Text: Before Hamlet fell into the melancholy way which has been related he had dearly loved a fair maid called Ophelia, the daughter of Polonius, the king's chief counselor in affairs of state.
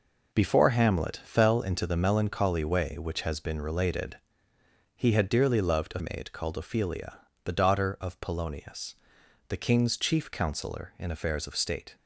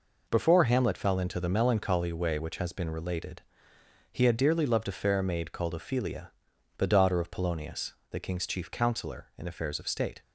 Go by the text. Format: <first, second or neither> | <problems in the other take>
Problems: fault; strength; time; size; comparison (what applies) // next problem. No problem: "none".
second | pauses between "related" and "he"; noticeable; at 4.1 s; 0.80 s long; noticeable in the second // skips "fair"; at 5.9 s